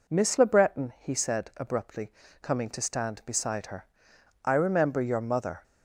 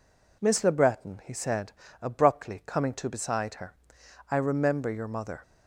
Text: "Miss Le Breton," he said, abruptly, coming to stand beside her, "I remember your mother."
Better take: first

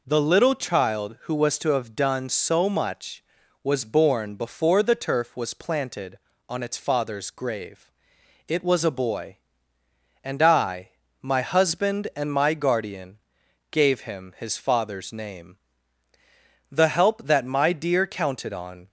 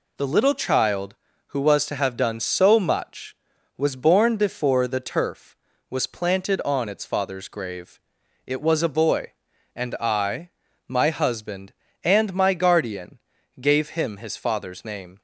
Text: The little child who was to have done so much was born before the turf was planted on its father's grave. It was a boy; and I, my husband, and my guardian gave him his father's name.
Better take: second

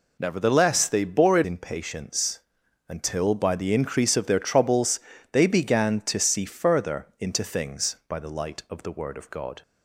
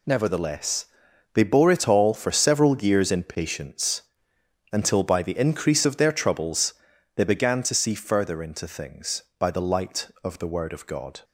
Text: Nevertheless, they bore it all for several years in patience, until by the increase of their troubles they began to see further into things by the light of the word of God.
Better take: second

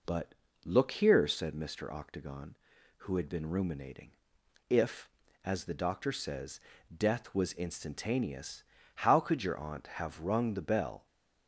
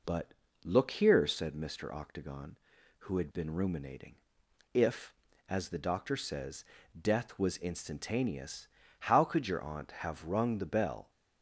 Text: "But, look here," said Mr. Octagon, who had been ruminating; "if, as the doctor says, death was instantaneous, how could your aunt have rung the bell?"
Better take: neither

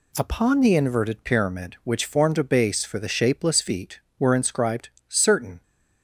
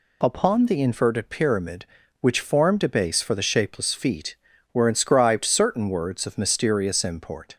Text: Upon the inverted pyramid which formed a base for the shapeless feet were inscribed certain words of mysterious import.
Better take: second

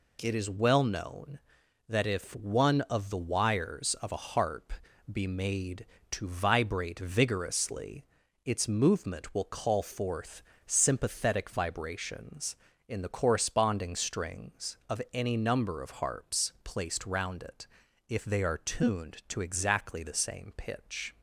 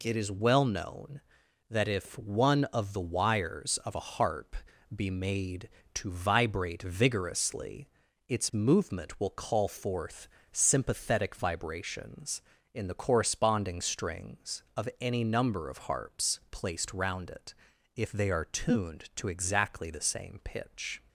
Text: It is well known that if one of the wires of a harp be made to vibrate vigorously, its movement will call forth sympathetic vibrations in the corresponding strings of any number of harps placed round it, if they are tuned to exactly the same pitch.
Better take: neither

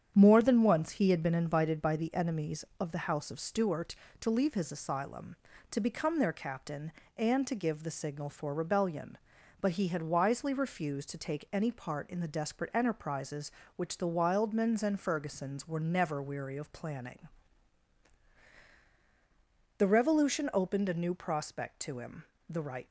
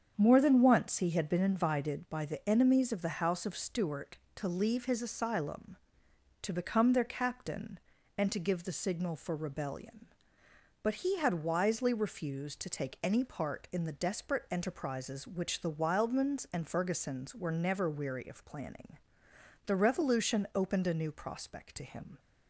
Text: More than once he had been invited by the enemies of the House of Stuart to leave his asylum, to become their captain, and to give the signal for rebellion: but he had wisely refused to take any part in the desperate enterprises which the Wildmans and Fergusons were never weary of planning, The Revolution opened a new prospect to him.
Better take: second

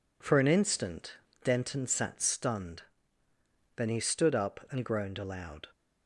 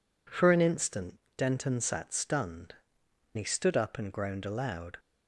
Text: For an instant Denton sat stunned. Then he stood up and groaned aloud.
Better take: first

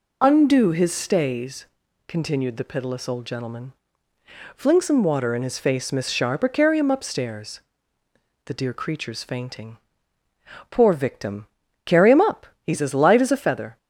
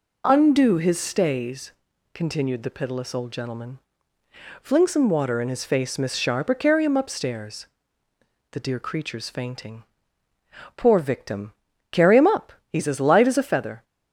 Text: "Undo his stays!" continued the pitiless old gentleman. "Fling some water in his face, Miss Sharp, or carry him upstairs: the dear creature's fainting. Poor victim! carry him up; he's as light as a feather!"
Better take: second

